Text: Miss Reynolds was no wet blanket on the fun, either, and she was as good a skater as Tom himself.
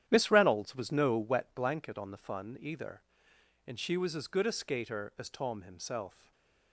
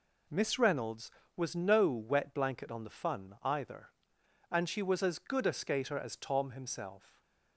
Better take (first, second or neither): second